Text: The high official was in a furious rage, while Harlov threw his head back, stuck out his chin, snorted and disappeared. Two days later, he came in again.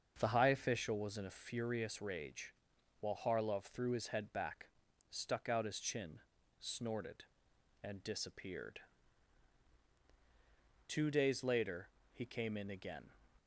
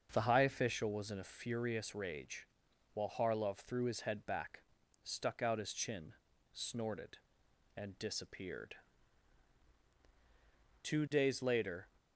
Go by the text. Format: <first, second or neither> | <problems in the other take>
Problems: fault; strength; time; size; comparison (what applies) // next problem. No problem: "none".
first | starts louder than the rest; until 1.1 s; 6.5 dB; also in the first // stops before "he came in again"; at 11.9 s